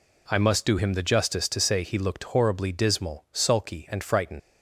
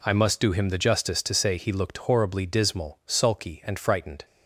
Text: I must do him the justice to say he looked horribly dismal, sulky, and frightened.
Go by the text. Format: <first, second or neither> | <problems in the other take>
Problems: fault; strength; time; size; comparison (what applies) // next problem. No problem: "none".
second | leaves "frightened" unfinished; at 4.3 s; 95 ms